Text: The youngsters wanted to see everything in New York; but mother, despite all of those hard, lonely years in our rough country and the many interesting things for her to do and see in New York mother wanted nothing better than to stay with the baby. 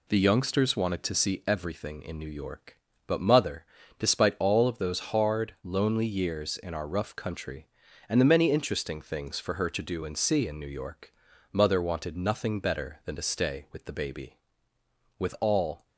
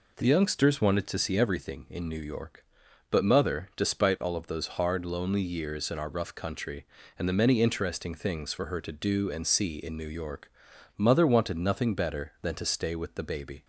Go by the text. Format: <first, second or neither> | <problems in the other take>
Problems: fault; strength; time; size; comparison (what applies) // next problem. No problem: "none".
second | pauses between "York" and "mother"; at 11.1 s; 0.38 s long; noticeable in the second // goes on to say "With all"; noticeable; from 15.1 s on; 0.70 s long